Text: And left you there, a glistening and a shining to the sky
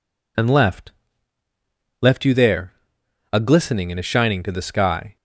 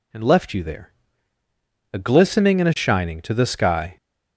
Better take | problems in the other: second | says "left" twice; at 2.0 s

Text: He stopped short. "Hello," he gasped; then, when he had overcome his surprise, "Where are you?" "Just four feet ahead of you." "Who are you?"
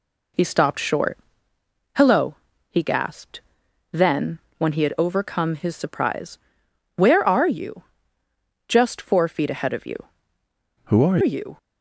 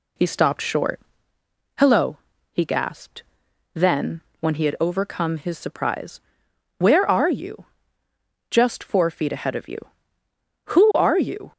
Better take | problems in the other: second | changes voice from "Who" to "are"; from 10.8 to 11.1 s; 0.3 s long

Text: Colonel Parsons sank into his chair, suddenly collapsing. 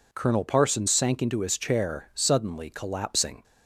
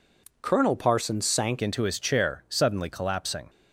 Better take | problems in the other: first | changes voice at "into"; from 1.6 s on; 1.8 s long

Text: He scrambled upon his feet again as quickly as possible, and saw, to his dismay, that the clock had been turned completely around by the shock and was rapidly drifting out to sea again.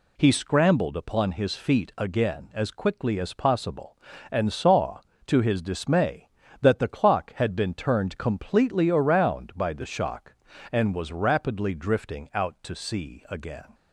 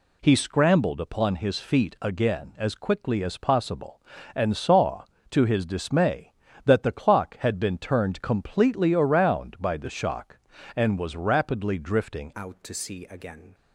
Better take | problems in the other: first | changes voice at "out"; from 12.3 s on; 1.2 s long

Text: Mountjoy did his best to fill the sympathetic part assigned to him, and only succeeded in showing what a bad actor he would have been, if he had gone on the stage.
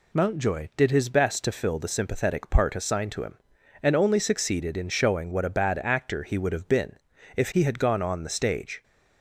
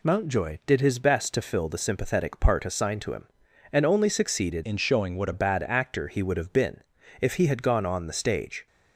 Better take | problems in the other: first | changes voice from "in" to "what"; from 4.6 to 5.3 s; 0.7 s long

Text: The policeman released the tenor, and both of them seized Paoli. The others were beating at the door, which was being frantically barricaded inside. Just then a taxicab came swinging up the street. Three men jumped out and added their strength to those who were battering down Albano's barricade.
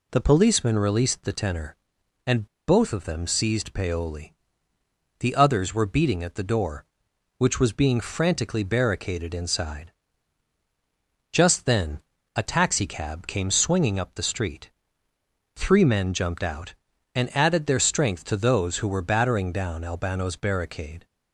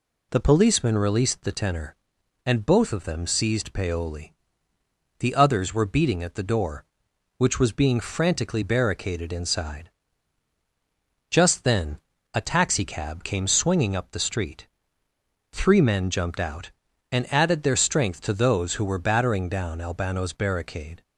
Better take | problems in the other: second | pauses between "and" and "both"; slight; at 2.4 s; 0.22 s long // pauses between "then" and "a"; slight; at 12.0 s; 0.34 s long; slight in the second

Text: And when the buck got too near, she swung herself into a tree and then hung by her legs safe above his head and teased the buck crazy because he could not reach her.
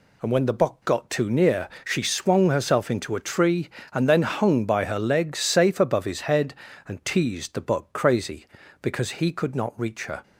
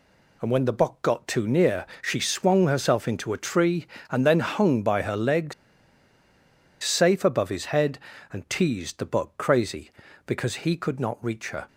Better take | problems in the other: first | pauses between "legs" and "safe"; strong; at 5.5 s; 1.2 s long

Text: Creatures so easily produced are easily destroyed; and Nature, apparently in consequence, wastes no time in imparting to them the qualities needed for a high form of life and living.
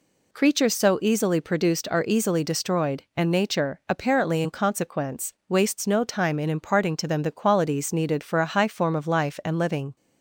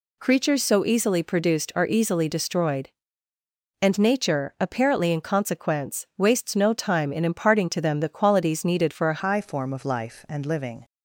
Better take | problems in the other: first | changes voice at "high"; from 9.1 s on; 1.7 s long

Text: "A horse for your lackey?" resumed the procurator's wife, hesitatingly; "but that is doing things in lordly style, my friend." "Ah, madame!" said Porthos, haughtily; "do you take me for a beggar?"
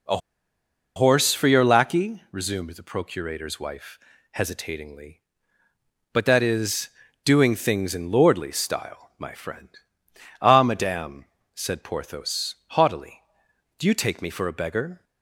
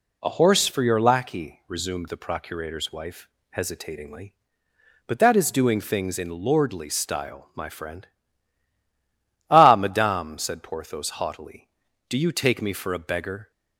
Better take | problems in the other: second | pauses between "A" and "horse"; noticeable; at 0.1 s; 0.78 s long // pauses between "is" and "doing"; slight; at 6.8 s; 0.36 s long

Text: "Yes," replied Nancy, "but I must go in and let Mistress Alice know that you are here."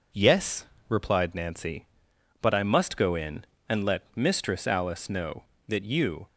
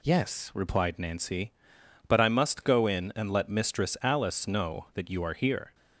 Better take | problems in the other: second | stops before "are here"; at 6.2 s

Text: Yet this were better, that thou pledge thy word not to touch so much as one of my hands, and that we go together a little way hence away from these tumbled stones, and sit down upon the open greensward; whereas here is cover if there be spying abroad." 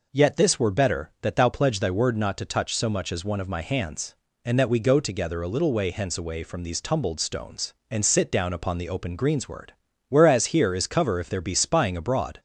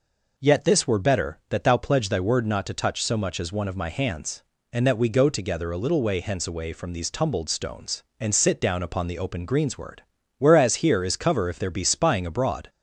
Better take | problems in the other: neither | none

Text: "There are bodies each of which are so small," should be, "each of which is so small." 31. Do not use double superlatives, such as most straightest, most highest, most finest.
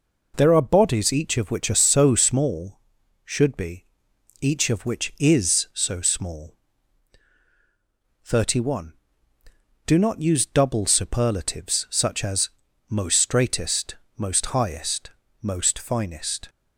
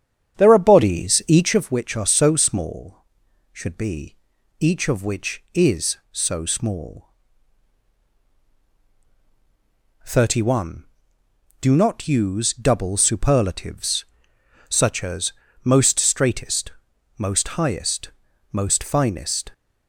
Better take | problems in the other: first | starts louder than the rest; strong; until 1.6 s; 8.5 dB // pauses between "as" and "most"; slight; at 15.3 s; 0.30 s long; also in the first

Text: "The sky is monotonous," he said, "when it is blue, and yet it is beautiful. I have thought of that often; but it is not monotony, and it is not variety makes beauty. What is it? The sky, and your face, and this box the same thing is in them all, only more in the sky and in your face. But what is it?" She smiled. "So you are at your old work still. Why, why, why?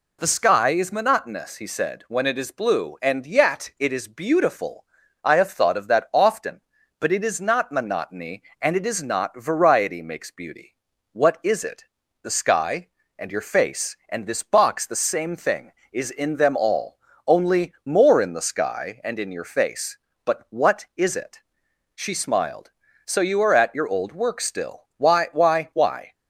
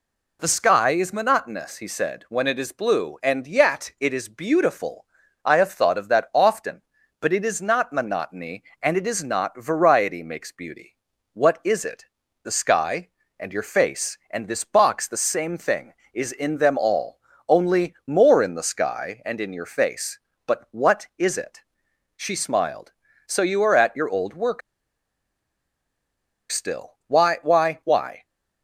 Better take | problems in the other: first | pauses between "work" and "still"; strong; at 24.6 s; 1.9 s long

